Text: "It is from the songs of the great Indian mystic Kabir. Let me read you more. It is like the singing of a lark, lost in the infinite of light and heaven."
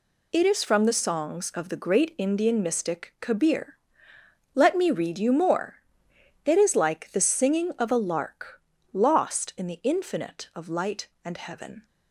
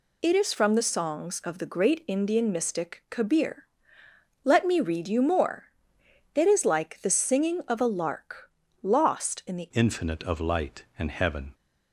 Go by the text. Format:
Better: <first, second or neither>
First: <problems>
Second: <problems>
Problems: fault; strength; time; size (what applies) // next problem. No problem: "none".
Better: first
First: none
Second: changes voice at "infinite"; from 9.7 s on; 1.8 s long